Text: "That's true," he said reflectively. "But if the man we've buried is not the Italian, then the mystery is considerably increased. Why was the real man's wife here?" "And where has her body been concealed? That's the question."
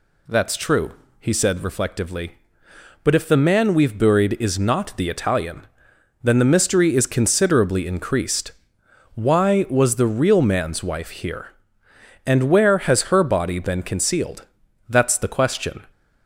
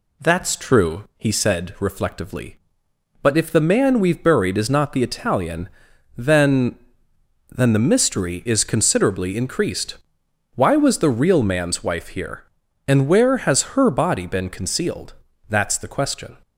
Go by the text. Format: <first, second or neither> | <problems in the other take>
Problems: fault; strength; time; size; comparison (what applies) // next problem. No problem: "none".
first | says "then" twice; at 7.4 s